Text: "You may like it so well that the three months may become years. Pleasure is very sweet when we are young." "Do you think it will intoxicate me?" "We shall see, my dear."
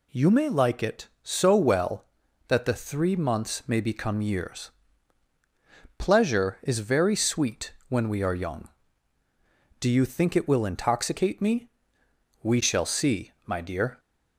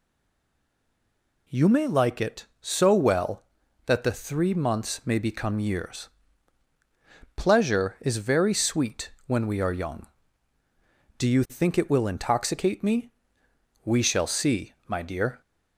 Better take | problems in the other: first | stays silent before the first word; noticeable; until 1.4 s; 1.4 s long // pauses between "sweet" and "when"; slight; at 9.1 s; 0.16 s long; slight in the first

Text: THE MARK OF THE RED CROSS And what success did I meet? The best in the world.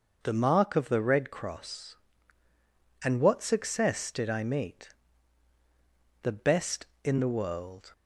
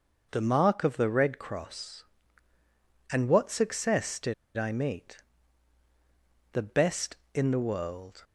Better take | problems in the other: first | pauses between "did" and "I"; slight; at 4.3 s; 0.23 s long

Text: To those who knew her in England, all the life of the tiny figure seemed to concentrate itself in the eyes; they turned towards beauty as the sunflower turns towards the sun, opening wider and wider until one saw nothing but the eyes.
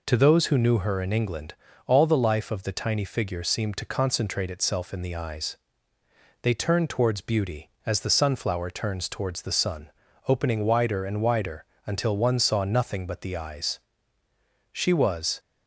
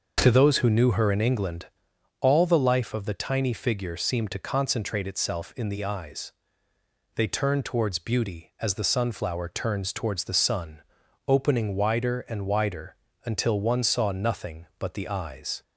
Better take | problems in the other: second | pauses between "wider" and "until"; slight; at 11.6 s; 0.22 s long; slight in the second // goes on to say "She was"; noticeable; from 14.7 s on; 0.66 s long

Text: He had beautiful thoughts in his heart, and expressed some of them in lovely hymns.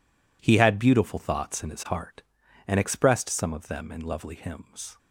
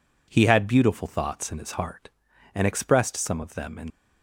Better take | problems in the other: first | stops before "lovely hymns"; at 3.8 s

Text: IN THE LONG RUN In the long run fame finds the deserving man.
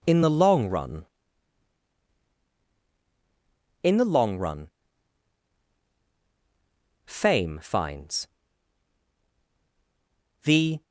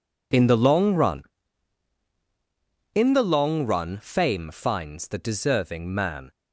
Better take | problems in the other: second | pauses between "run" and "fame"; strong; at 4.6 s; 2.3 s long // pauses between "finds" and "the"; strong; at 8.2 s; 2.1 s long // stops before "deserving man"; at 10.8 s

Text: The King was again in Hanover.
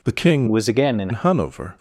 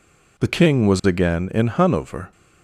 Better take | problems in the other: second | changes voice from "was" to "in"; from 0.4 to 1.0 s; 0.6 s long

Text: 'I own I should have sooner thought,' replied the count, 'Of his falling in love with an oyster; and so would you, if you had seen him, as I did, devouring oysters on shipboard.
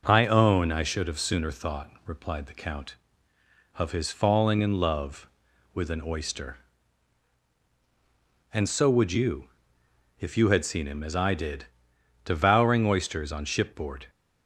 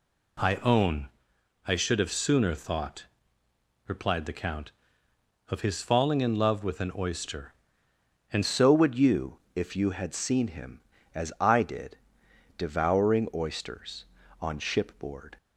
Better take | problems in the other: first | pauses between "own" and "I"; noticeable; at 1.0 s; 0.58 s long // changes voice at "so"; from 8.4 s on; 6.9 s long

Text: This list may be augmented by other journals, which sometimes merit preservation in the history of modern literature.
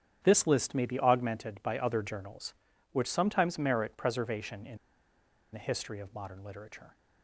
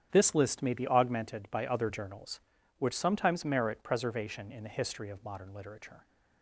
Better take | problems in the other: second | starts louder than the rest; strong; until 1.2 s; 9 dB; strong in the second // pauses between "in" and "the"; noticeable; at 4.7 s; 0.75 s long

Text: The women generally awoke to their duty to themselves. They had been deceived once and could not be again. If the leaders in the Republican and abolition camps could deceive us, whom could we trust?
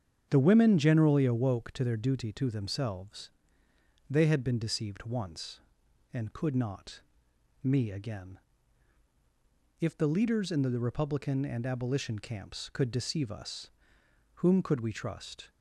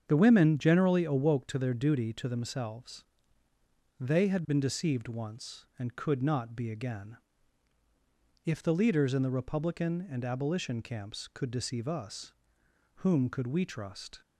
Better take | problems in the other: second | starts louder than the rest; strong; until 1.3 s; 8 dB; strong in the second // says "me" for "be"; at 7.6 s

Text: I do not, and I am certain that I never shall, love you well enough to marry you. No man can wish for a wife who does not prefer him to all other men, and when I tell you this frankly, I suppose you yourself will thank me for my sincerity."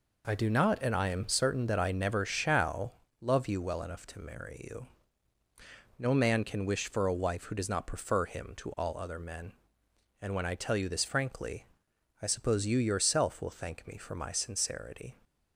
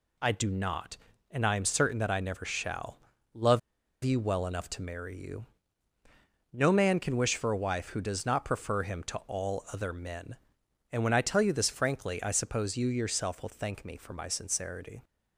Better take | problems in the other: first | pauses between "love" and "you"; at 3.5 s; 0.43 s long

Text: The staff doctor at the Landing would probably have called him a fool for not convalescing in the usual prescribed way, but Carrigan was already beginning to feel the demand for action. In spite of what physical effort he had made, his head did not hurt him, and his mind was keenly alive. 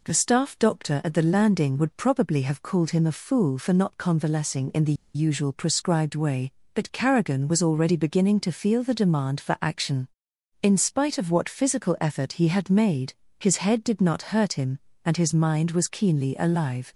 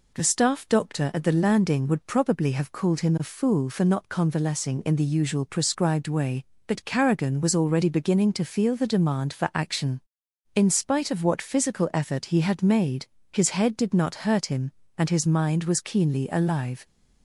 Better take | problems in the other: second | pauses between "the" and "usual"; slight; at 4.9 s; 0.21 s long

